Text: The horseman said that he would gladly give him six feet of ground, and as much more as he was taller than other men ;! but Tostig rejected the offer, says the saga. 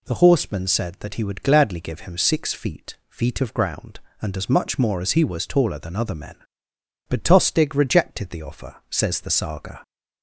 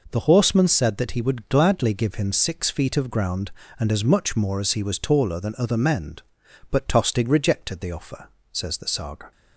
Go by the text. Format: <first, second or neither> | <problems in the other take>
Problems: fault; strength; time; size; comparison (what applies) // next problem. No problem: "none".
second | says "feet" twice; at 3.0 s